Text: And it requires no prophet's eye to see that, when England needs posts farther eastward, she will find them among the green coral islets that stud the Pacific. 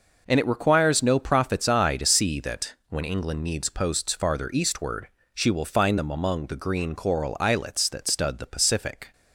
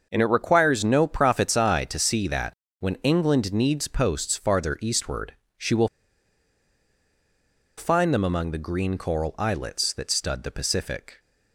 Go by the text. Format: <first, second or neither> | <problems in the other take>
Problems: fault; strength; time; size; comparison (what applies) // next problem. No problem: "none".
first | starts louder than the rest; until 1.1 s; 6 dB // pauses between "will" and "find"; strong; at 5.8 s; 1.8 s long